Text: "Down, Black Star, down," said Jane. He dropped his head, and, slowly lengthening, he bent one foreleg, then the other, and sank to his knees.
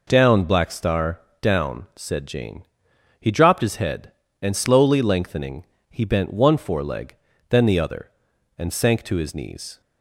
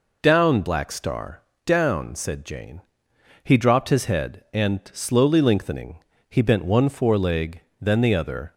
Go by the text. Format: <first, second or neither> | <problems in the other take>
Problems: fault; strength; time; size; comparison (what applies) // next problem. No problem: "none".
first | stops before "and sank to his knees"; at 8.5 s